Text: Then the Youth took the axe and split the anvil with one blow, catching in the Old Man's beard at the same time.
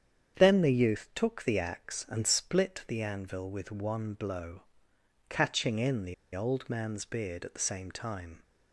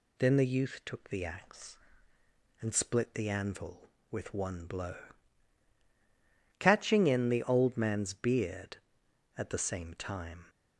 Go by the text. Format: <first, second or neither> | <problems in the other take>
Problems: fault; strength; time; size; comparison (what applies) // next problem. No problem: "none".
second | starts louder than the rest; strong; until 1.4 s; 8 dB // pauses between "the" and "Old"; slight; at 6.1 s; 0.20 s long